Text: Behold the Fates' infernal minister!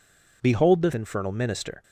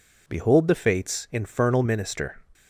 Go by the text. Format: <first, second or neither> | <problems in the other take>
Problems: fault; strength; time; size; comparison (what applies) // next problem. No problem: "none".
second | skips "Fates"; at 0.9 s